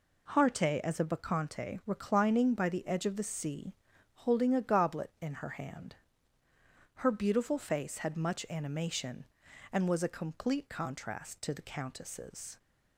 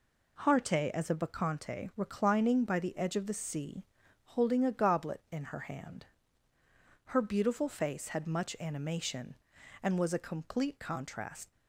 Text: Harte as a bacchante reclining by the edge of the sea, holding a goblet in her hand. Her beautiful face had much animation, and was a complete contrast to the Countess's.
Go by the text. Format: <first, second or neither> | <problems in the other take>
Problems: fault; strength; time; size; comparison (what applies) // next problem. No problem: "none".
first | stops before "to the Countess's"; at 11.5 s